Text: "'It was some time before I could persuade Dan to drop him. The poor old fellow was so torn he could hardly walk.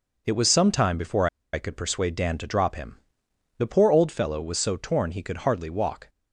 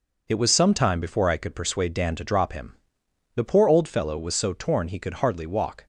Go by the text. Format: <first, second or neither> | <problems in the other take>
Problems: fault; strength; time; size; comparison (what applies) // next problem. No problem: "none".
second | pauses between "before" and "I"; slight; at 1.2 s; 0.26 s long